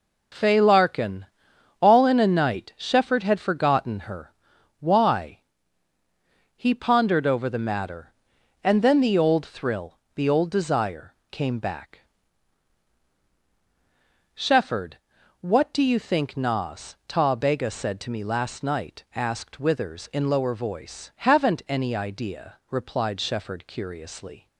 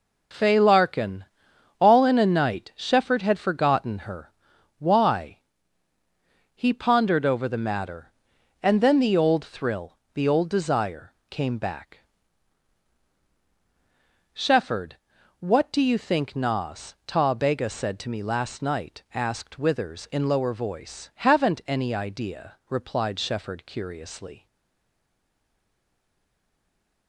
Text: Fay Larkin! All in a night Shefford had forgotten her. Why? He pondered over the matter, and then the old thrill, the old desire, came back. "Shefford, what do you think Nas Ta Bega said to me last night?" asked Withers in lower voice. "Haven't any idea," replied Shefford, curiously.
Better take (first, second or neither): first